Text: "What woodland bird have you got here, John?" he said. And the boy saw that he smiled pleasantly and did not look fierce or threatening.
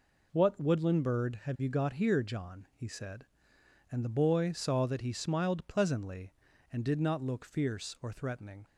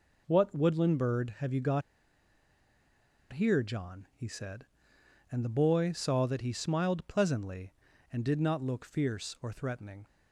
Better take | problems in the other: first | pauses between "got" and "here"; strong; at 1.8 s; 1.5 s long

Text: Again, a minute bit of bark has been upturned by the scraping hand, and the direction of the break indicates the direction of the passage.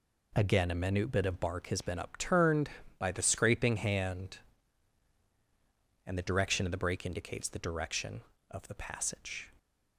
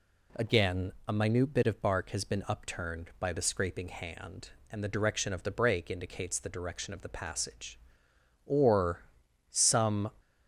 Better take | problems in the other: first | goes on to say "Or some"; from 8.4 s on; 1.6 s long

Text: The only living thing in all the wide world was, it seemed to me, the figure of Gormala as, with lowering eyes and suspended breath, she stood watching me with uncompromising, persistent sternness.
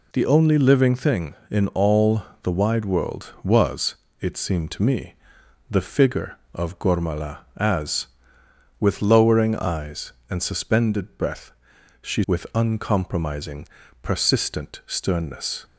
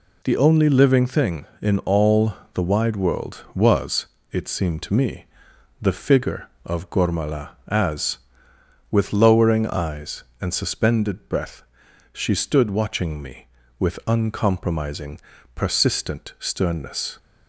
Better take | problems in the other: second | pauses between "all" and "the"; slight; at 2.2 s; 0.20 s long; slight in the second // skips "stood watching me"; at 12.2 s

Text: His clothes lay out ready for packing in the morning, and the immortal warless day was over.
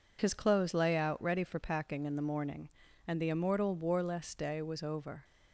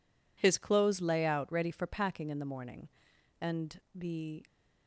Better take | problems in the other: first | stops before "immortal warless day was over"; at 4.4 s

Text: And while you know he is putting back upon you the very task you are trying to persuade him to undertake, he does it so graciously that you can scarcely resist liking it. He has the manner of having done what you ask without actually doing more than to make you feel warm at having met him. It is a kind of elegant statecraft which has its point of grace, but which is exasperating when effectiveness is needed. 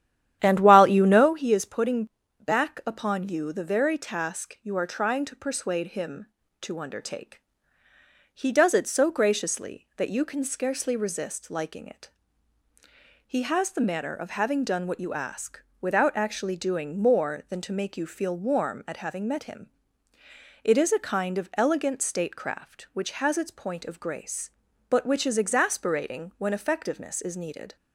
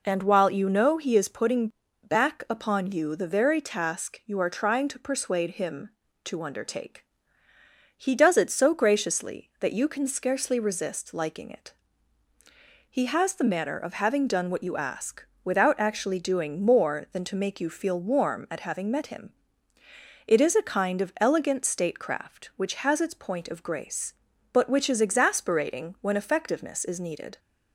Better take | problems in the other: second | starts louder than the rest; strong; until 1.3 s; 11 dB // pauses between "putting" and "back"; slight; at 2.0 s; 0.36 s long; slight in the second // pauses between "ask" and "without"; slight; at 15.6 s; 0.20 s long; slight in the second

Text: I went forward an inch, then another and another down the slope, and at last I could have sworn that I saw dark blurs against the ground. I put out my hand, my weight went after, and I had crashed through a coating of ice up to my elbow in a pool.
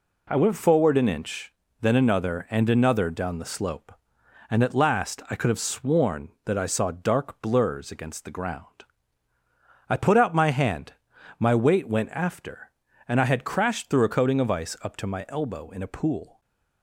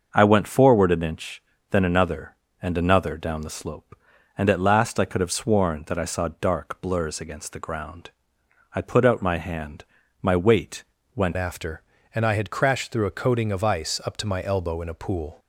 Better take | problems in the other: first | starts louder than the rest; until 1.1 s; 6.5 dB // pauses between "weight" and "went"; slight; at 10.8 s; 0.30 s long // changes voice at "after"; from 11.3 s on; 4.0 s long

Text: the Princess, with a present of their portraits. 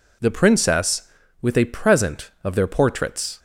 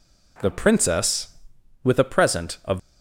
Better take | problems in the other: first | stops before "their portraits"; at 2.7 s

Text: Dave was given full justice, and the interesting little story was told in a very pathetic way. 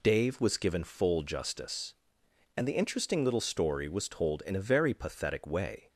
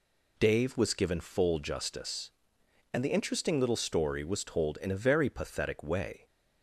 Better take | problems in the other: neither | none

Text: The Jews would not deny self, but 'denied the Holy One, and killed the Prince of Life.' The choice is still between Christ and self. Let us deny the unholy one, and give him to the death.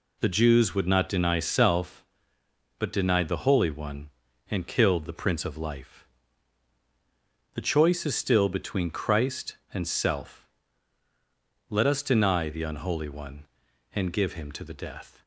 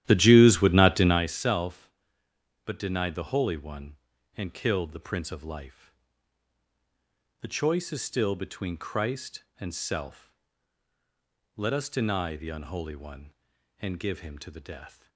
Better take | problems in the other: first | starts louder than the rest; strong; until 1.3 s; 12.5 dB

